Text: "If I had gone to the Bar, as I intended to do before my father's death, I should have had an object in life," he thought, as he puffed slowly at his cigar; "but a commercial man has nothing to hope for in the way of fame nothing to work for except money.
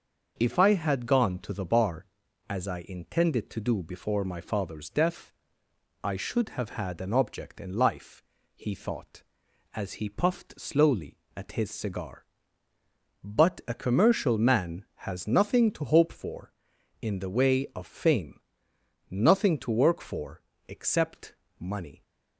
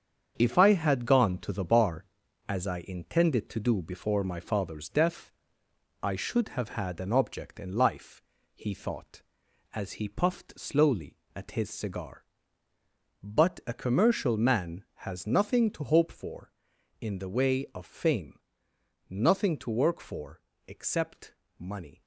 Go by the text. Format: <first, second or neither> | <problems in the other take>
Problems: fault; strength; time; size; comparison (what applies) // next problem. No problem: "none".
first | gets quieter; strong; throughout; 7 dB // starts louder than the rest; strong; until 1.3 s; 7.5 dB; noticeable in the first // pauses between "fame" and "nothing"; noticeable; at 18.4 s; 0.68 s long; noticeable in the first // pauses between "for" and "except"; slight; at 20.4 s; 0.26 s long; slight in the first // pauses between "except" and "money"; slight; at 21.3 s; 0.24 s long; slight in the first